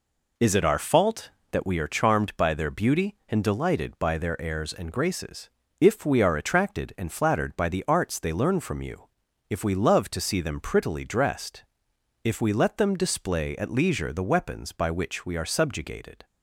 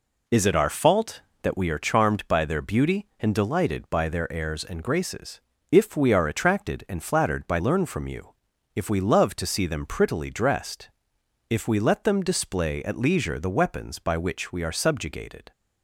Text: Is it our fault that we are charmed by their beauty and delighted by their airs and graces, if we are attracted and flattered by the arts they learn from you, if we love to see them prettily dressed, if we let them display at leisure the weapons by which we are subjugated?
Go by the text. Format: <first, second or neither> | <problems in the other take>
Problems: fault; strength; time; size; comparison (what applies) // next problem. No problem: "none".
first | skips "the arts they"; at 7.6 s